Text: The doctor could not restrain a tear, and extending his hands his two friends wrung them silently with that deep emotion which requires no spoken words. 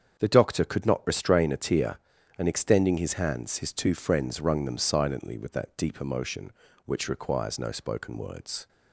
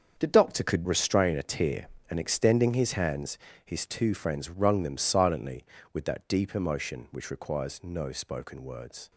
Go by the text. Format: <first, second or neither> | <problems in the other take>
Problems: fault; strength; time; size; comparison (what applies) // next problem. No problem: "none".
first | starts louder than the rest; until 1.2 s; 7 dB; strong in the first // skips "not"; at 0.8 s // pauses between "hands" and "his"; slight; at 3.3 s; 0.30 s long